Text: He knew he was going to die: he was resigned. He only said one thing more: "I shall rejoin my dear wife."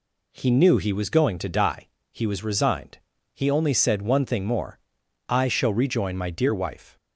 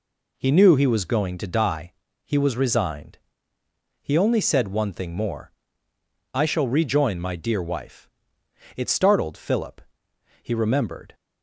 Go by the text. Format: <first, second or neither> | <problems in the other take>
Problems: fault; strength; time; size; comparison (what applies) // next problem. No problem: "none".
first | goes on to say "It startled Philip He remembered"; strong; from 8.7 s on; 2.4 s long